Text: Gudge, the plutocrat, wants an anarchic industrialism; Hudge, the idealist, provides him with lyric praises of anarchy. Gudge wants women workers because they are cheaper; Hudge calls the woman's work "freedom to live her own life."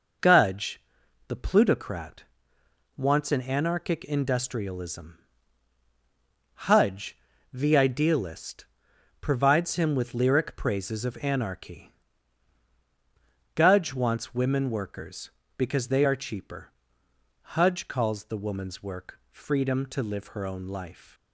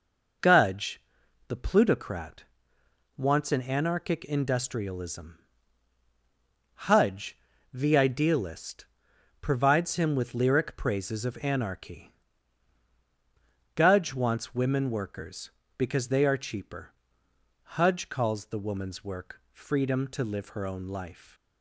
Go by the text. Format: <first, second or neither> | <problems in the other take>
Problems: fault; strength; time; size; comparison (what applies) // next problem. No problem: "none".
neither | none